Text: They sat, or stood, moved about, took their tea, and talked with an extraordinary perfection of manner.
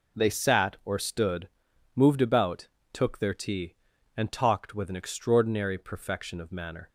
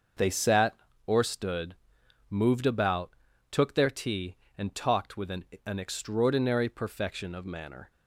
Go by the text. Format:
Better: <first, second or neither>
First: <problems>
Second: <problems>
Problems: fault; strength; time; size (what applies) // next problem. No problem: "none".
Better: first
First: none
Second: starts louder than the rest; noticeable; until 1.5 s; 6 dB // says "an" twice; at 5.6 s